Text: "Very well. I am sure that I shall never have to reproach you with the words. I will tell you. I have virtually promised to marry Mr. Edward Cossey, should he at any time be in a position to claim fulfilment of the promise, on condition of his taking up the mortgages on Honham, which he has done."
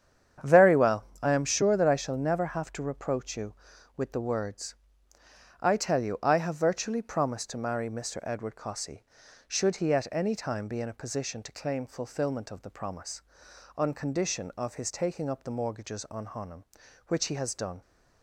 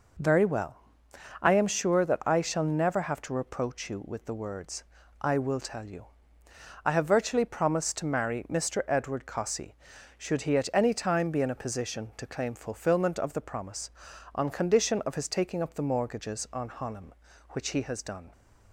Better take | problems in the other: second | starts louder than the rest; strong; until 1.6 s; 8.5 dB // skips "will"; at 5.7 s

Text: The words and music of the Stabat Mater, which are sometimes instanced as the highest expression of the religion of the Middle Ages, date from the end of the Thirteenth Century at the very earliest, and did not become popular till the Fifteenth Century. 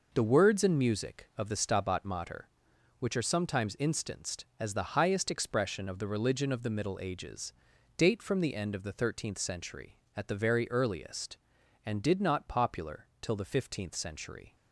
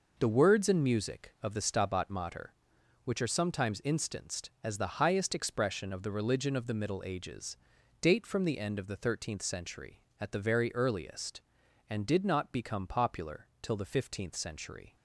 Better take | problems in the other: second | skips "become"; at 12.4 s

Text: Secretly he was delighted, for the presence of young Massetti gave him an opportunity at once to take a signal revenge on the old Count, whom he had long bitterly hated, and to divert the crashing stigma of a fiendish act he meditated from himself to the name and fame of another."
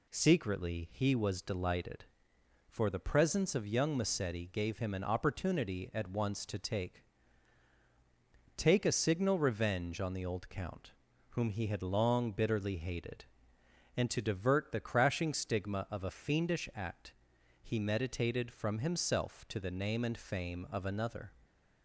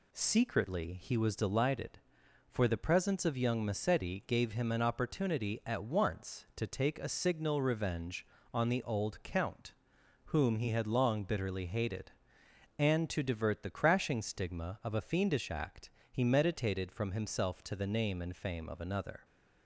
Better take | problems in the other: second | says "take" twice; at 8.5 s // pauses between "act" and "he"; noticeable; at 17.1 s; 0.50 s long; slight in the second

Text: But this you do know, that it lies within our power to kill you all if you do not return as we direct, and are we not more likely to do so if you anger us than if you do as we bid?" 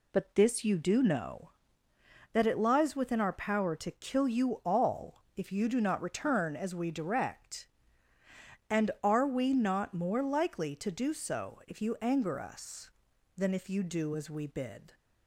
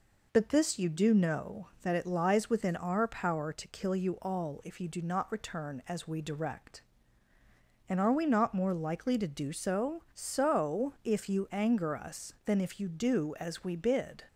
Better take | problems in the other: first | says "so" twice; at 10.1 s

